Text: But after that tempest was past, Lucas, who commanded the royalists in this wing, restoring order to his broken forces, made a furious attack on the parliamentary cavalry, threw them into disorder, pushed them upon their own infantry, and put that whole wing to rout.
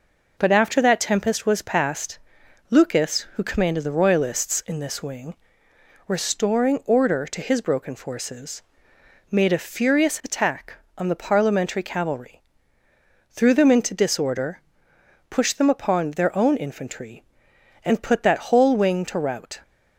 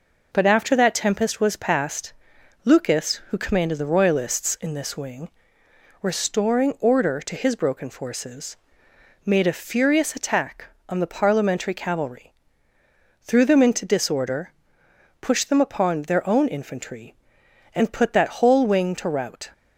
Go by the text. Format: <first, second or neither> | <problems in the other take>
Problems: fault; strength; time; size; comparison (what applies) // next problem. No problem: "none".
neither | none